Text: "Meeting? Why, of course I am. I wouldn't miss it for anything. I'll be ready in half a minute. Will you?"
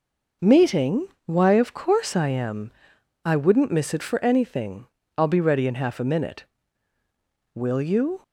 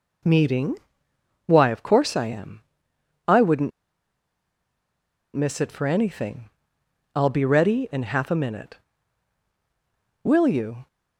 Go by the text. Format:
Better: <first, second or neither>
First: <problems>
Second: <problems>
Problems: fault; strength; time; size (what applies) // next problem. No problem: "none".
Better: first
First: none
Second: pauses between "wouldn't" and "miss"; strong; at 3.7 s; 1.6 s long